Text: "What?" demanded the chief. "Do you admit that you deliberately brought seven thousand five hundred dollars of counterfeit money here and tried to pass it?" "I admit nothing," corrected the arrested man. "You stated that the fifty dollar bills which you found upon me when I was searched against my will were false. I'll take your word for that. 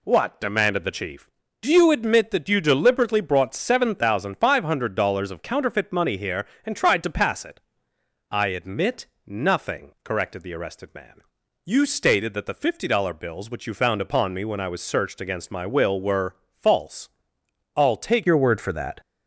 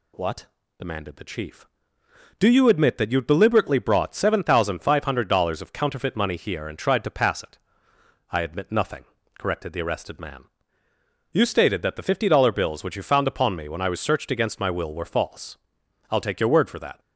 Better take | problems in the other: second | pauses between "admit" and "nothing"; slight; at 9.0 s; 0.18 s long // pauses between "were" and "false"; slight; at 16.3 s; 0.20 s long // changes voice at "your"; from 18.2 s on; 0.8 s long

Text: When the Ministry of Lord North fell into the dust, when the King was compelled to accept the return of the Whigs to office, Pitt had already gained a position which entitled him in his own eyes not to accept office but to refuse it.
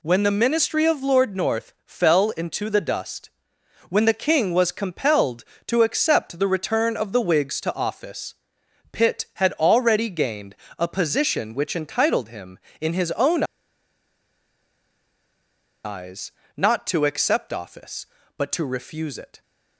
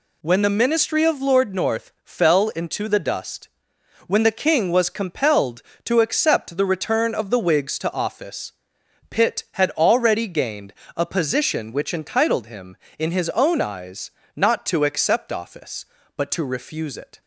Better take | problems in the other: second | pauses between "gained" and "a"; slight; at 10.5 s; 0.24 s long; slight in the second // pauses between "own" and "eyes"; strong; at 13.4 s; 2.4 s long // pauses between "eyes" and "not"; slight; at 16.3 s; 0.24 s long; slight in the second

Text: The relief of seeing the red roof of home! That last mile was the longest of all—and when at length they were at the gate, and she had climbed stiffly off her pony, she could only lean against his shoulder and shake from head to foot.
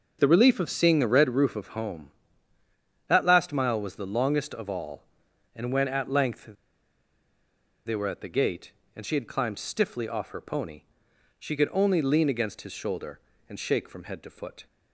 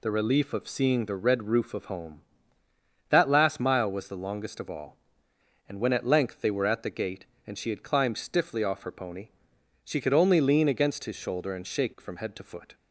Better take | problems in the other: second | starts louder than the rest; until 1.2 s; 6 dB // pauses between "length" and "they"; strong; at 6.4 s; 1.4 s long

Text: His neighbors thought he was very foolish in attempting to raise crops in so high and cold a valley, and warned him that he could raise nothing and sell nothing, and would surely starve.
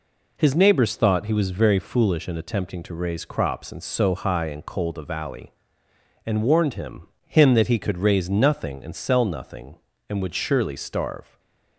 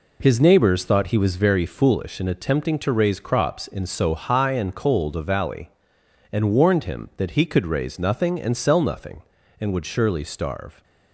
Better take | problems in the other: second | says "him" twice; at 7.2 s // stays silent after the last word; slight; from 11.2 s on; 0.5 s long

